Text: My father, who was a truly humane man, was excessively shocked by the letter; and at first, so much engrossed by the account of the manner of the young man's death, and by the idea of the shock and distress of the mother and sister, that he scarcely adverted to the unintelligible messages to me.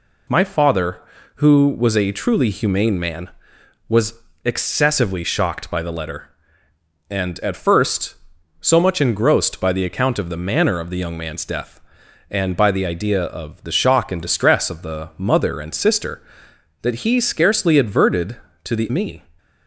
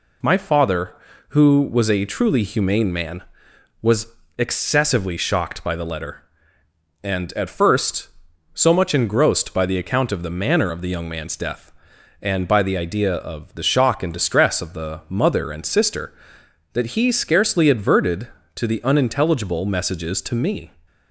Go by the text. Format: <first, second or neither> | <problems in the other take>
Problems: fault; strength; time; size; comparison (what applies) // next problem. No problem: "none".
second | pauses between "was" and "excessively"; slight; at 4.1 s; 0.30 s long; slight in the second // skips "unintelligible messages to"; at 18.8 s